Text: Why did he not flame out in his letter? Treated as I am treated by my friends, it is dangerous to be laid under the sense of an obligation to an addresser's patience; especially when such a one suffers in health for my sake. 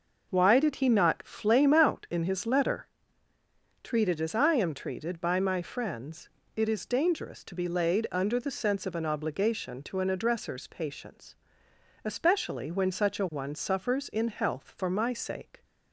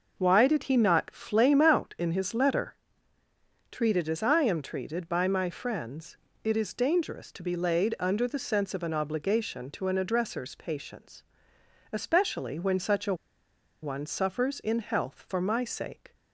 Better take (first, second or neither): first